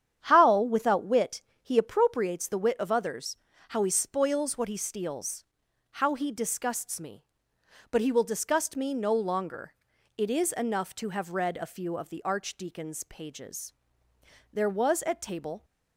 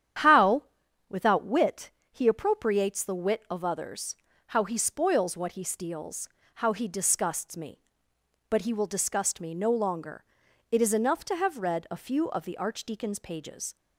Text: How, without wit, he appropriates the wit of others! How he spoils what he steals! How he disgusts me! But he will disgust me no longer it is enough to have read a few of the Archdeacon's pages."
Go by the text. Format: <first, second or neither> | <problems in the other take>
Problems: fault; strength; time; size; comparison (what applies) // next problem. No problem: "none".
second | starts louder than the rest; strong; until 1.2 s; 9 dB; strong in the second // pauses between "longer" and "it"; at 9.7 s; 0.44 s long; noticeable in the second // goes on to say "There was at table"; noticeable; from 14.5 s on; 1.1 s long